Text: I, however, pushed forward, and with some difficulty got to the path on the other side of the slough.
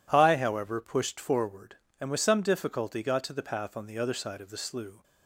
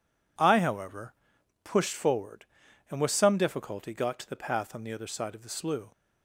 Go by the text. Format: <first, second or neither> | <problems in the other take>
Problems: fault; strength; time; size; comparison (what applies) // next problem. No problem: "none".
neither | none